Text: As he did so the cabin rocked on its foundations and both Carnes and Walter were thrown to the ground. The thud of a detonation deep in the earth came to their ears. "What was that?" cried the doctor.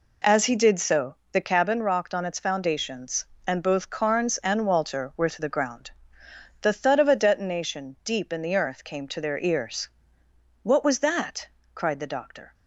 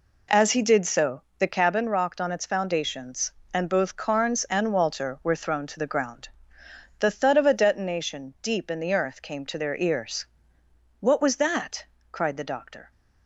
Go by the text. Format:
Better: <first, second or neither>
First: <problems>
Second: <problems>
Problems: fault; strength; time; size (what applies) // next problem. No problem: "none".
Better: second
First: pauses between "so" and "the"; slight; at 1.1 s; 0.16 s long // skips "thrown"; at 5.2 s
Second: pauses between "so" and "the"; slight; at 1.2 s; 0.16 s long